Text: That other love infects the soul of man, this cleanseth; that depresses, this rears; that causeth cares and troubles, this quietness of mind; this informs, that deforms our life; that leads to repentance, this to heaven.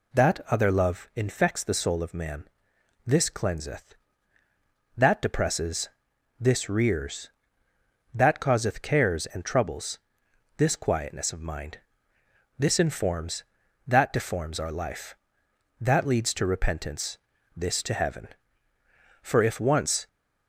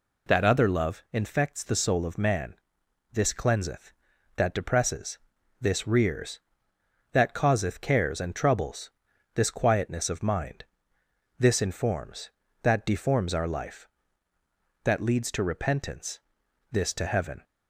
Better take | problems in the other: second | goes on to say "For if once"; noticeable; from 19.2 s on; 0.86 s long

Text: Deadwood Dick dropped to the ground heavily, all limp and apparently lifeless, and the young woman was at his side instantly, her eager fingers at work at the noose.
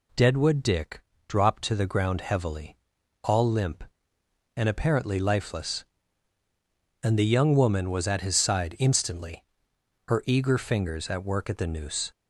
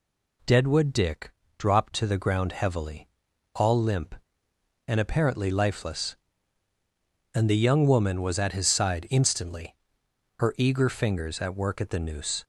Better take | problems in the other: neither | pauses between "Dick" and "dropped"; slight; the same in both

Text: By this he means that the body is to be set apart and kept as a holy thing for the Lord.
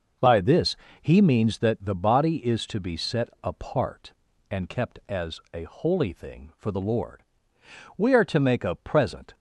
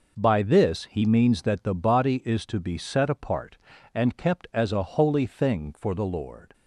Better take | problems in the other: second | pauses between "this" and "he"; slight; at 0.7 s; 0.24 s long // pauses between "set" and "apart"; slight; at 3.2 s; 0.16 s long // goes on to say "We are to make a present"; from 7.9 s on; 1.3 s long

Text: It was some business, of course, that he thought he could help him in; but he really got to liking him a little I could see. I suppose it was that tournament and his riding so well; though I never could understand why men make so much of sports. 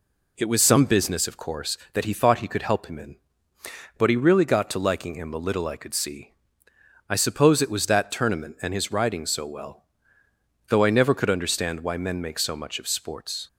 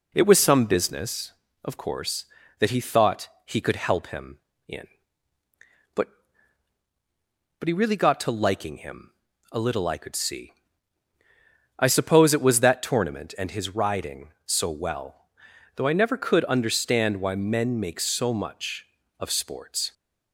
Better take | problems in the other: first | pauses between "thought" and "he"; slight; at 3.2 s; 0.18 s long // says "but" twice; at 7.5 s // pauses between "him" and "a"; at 9.1 s; 0.40 s long

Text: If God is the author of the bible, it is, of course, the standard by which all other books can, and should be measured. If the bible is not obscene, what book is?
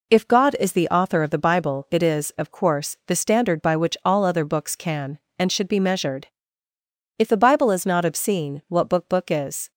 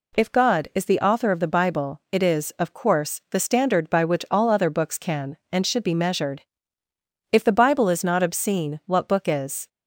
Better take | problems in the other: second | says "book" twice; at 9.0 s

